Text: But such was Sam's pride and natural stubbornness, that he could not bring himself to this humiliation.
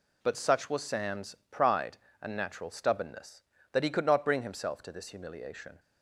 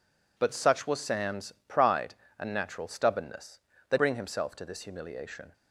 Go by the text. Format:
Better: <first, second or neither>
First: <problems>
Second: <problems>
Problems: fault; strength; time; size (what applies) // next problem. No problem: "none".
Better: first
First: pauses between "Sam's" and "pride"; slight; at 1.3 s; 0.16 s long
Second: pauses between "Sam's" and "pride"; slight; at 1.5 s; 0.16 s long // skips "he could not"; at 3.9 s